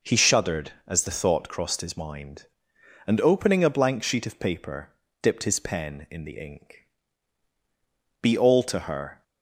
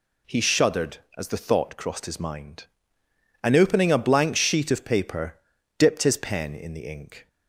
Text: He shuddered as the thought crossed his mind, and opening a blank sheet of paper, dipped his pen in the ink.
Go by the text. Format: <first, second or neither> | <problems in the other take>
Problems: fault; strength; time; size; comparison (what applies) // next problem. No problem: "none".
second | goes on to say "Be all to her"; noticeable; from 8.2 s on; 1.0 s long